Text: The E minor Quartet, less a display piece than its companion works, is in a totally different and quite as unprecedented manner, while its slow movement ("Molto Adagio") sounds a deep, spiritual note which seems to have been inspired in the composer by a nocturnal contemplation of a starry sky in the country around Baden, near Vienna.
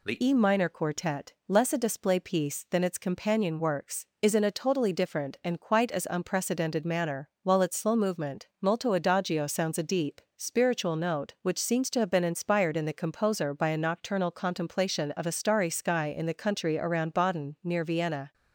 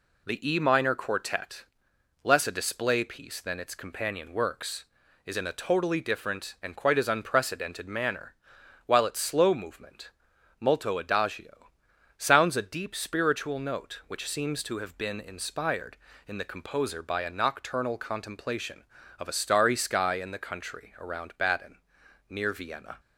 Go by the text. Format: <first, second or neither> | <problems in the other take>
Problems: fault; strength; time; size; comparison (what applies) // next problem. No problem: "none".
second | changes voice at "E"; from 0.2 s on; 18.1 s long